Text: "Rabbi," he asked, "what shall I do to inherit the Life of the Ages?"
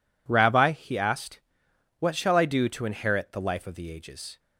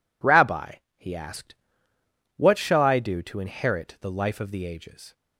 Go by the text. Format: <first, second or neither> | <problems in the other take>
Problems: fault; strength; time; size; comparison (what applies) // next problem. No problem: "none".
neither | none